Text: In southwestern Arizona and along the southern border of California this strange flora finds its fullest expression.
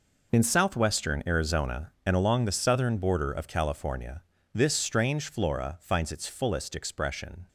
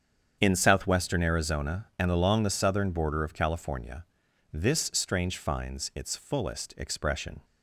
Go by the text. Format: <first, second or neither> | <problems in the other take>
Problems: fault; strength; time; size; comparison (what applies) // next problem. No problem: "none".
first | starts louder than the rest; strong; until 1.4 s; 8 dB // pauses between "California" and "this"; noticeable; at 4.0 s; 0.48 s long; slight in the first // skips "flora"; at 5.3 s